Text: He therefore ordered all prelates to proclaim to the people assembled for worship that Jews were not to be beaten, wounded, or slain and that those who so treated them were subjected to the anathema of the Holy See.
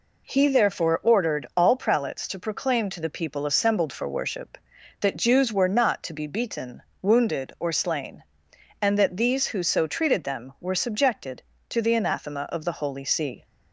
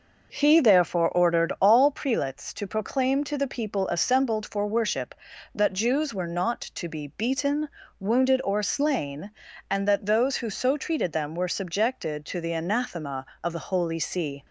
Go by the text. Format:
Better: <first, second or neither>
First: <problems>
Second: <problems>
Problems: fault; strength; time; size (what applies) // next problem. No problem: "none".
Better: second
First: says "these" for "those"; at 9.1 s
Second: none